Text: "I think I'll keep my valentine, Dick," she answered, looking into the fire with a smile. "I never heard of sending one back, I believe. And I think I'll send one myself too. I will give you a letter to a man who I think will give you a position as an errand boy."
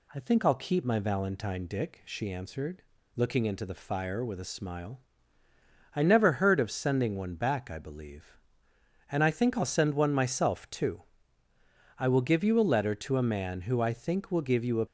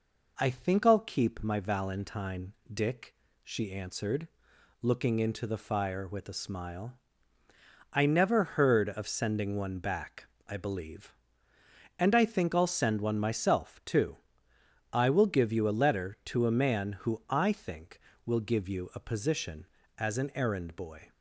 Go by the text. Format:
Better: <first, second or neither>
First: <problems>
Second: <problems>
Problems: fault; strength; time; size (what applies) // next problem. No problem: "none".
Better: second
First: stops before "position as an errand boy"; at 14.8 s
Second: none